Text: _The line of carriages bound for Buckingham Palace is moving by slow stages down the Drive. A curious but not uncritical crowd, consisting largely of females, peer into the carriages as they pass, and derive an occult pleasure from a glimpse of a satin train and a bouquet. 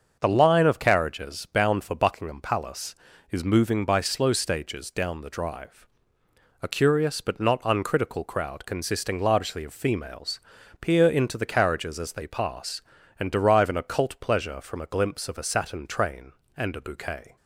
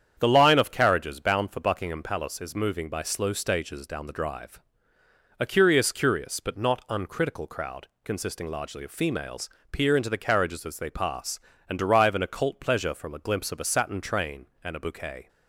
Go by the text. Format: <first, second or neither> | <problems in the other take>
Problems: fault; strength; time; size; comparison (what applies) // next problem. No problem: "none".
first | starts louder than the rest; strong; until 1.2 s; 8.5 dB; also in the first // says "curious" twice; at 5.9 s